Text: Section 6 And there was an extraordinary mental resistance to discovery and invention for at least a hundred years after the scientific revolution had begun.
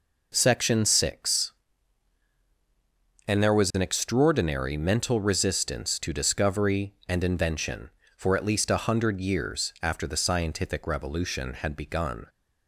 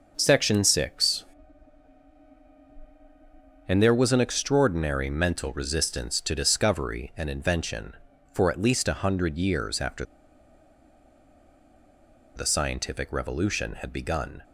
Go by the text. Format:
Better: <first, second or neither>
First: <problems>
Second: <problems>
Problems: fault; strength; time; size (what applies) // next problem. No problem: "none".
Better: first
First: none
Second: pauses between "after" and "the"; strong; at 10.0 s; 2.3 s long